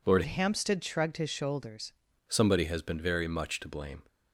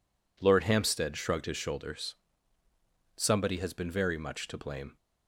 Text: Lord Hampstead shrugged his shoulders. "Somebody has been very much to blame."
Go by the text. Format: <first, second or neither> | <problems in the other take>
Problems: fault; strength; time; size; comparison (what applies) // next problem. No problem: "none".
second | changes voice from "Hampstead" to "shoulders"; from 0.2 to 1.9 s; 1.7 s long